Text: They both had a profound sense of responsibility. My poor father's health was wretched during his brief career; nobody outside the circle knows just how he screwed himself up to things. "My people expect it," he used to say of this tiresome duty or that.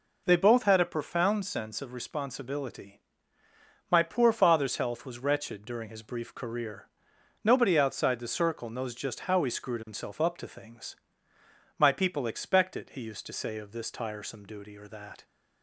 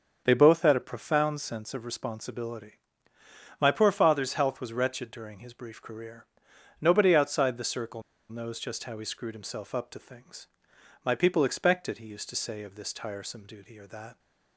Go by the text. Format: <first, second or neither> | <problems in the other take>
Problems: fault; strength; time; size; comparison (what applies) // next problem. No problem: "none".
first | starts louder than the rest; until 1.2 s; 7 dB // pauses between "circle" and "knows"; slight; at 8.0 s; 0.28 s long